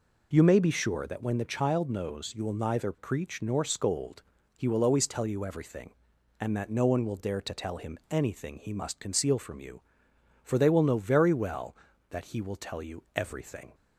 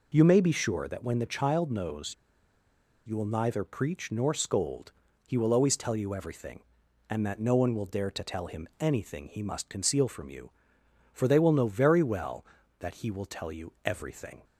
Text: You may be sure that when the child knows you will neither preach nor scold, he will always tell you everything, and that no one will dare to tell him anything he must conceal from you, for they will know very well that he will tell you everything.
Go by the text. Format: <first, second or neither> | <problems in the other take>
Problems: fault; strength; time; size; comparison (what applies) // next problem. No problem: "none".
first | pauses between "knows" and "you"; noticeable; at 2.1 s; 0.92 s long